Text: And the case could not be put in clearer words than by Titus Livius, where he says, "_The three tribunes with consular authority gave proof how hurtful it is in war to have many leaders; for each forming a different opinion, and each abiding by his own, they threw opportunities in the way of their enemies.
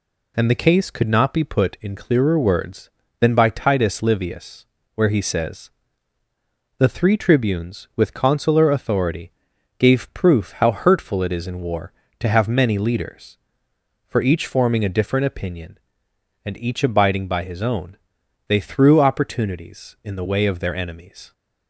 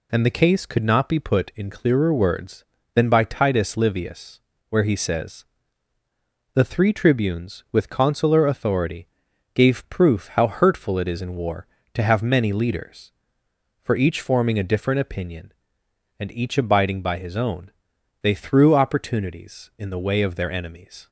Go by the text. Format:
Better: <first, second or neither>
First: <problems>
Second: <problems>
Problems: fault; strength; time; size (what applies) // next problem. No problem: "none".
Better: neither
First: pauses between "authority" and "gave"; noticeable; at 9.2 s; 0.48 s long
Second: pauses between "authority" and "gave"; noticeable; at 9.0 s; 0.48 s long